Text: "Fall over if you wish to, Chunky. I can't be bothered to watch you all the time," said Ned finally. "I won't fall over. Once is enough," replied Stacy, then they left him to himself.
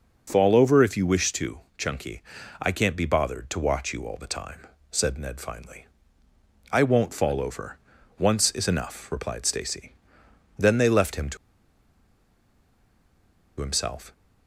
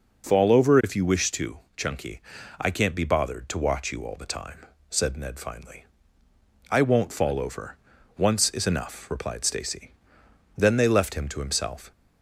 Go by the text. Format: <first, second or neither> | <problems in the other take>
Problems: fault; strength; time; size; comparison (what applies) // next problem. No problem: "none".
second | pauses between "to" and "himself"; strong; at 11.3 s; 2.2 s long